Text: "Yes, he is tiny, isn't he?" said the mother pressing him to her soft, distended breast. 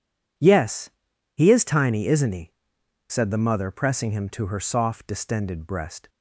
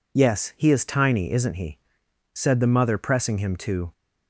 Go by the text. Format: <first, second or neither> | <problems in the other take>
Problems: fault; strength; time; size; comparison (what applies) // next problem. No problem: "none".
first | stops before "her soft distended breast"; at 3.9 s